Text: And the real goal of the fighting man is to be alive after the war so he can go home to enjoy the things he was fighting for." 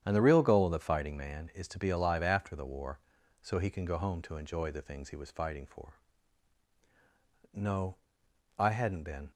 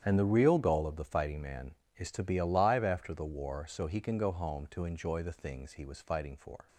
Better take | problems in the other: second | starts louder than the rest; strong; until 1.0 s; 9 dB; strong in the second // goes on to say "No I hadn't been"; strong; from 7.5 s on; 1.7 s long

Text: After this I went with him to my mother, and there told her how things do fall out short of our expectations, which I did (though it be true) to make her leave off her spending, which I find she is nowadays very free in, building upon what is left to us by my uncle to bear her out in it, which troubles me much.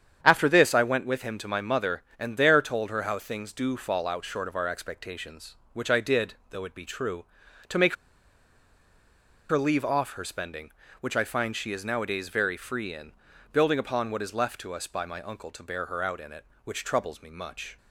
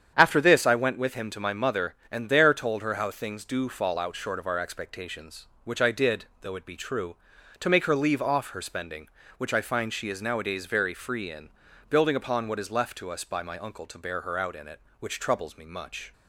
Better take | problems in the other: second | starts louder than the rest; strong; until 1.2 s; 8.5 dB; strong in the second // pauses between "make" and "her"; strong; at 7.9 s; 1.5 s long

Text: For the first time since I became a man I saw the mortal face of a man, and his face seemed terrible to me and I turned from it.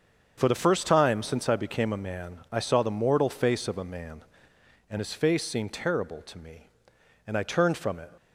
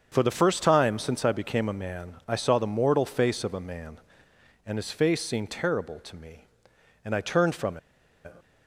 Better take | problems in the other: first | starts louder than the rest; until 1.1 s; 7 dB; also in the first // pauses between "from" and "it"; noticeable; at 7.7 s; 0.47 s long

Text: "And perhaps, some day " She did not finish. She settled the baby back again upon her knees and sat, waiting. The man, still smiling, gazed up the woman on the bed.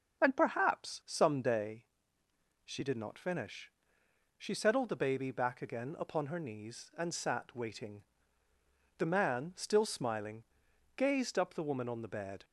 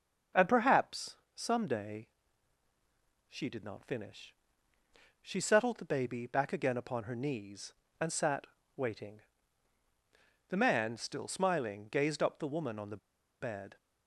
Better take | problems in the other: first | starts louder than the rest; noticeable; until 1.5 s; 6 dB; also in the first // pauses between "the" and "bed"; at 12.9 s; 0.43 s long

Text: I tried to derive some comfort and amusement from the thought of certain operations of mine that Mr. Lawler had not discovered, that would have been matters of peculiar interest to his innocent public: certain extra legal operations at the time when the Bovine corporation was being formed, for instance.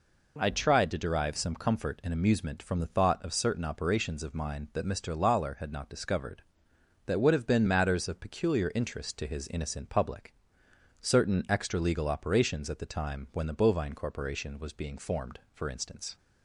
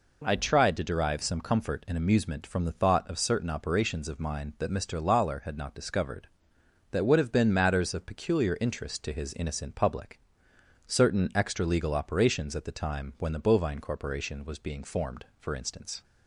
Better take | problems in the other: neither | none

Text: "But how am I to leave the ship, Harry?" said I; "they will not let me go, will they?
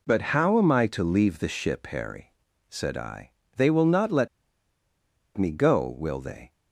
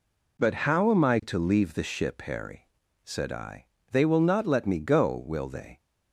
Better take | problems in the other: second | pauses between "let" and "me"; at 4.2 s; 1.0 s long

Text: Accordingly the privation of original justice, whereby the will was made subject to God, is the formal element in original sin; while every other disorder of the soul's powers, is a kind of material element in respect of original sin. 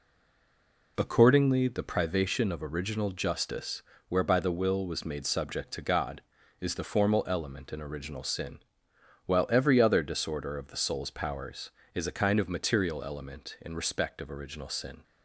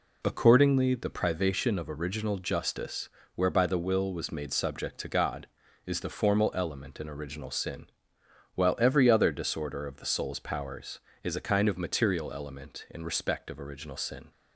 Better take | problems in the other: second | stays silent before the first word; slight; until 0.9 s; 0.9 s long

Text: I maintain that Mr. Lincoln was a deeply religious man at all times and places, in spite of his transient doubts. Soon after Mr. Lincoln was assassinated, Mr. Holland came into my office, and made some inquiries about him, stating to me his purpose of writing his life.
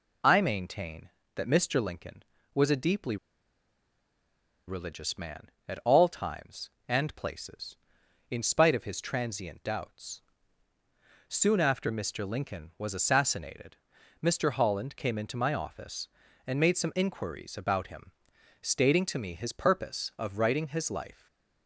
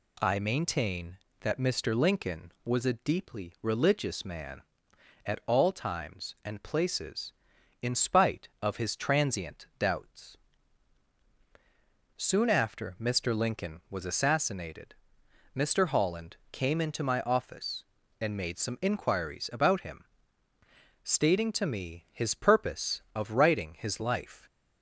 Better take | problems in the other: second | pauses between "deeply" and "religious"; strong; at 3.1 s; 1.5 s long // stays silent after the last word; slight; from 21.1 s on; 0.5 s long

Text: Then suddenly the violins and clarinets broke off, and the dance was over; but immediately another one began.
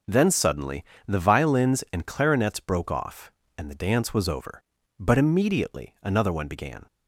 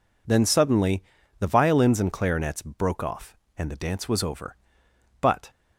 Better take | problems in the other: first | pauses between "suddenly" and "the"; slight; at 1.0 s; 0.36 s long; slight in the first // stops before "immediately another one began"; at 5.4 s

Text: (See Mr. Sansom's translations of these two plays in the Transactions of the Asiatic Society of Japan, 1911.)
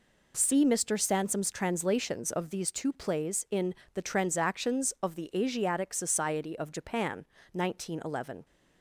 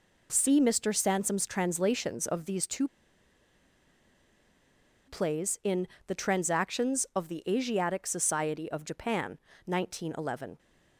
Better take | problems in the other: first | pauses between "two" and "plays"; strong; at 2.8 s; 2.2 s long // pauses between "in" and "the"; slight; at 5.8 s; 0.22 s long; slight in the first

